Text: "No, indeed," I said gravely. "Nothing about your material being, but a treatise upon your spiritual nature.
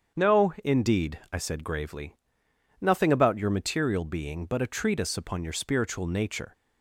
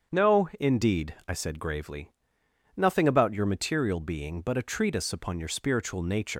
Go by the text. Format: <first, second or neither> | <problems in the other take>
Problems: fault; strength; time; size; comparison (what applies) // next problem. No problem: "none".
first | starts louder than the rest; strong; until 1.3 s; 7.5 dB; strong in the first // leaves "nature" unfinished; at 6.3 s; 80 ms